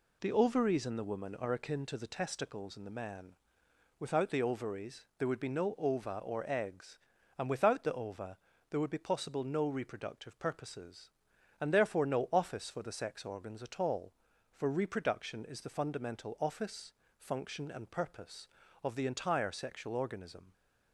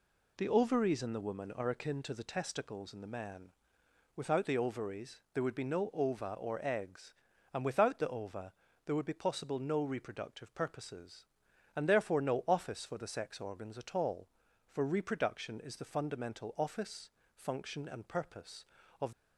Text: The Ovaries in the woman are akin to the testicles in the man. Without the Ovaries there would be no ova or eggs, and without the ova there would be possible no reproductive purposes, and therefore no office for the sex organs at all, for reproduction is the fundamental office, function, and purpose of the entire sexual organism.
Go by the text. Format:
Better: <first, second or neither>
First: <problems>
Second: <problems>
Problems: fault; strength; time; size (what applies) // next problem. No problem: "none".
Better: first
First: pauses between "ova" and "there"; slight; at 8.3 s; 0.32 s long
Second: pauses between "ova" and "there"; slight; at 8.5 s; 0.32 s long // stops before "the entire sexual organism"; at 19.1 s